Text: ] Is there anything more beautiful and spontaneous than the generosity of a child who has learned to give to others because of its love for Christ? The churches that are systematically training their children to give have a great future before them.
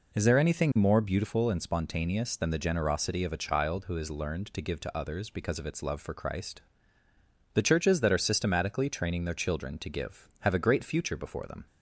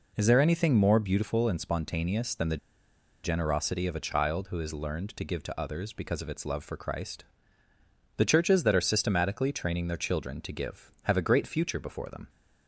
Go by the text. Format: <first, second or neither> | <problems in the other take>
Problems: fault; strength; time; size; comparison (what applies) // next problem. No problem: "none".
first | pauses between "the" and "generosity"; noticeable; at 2.5 s; 0.67 s long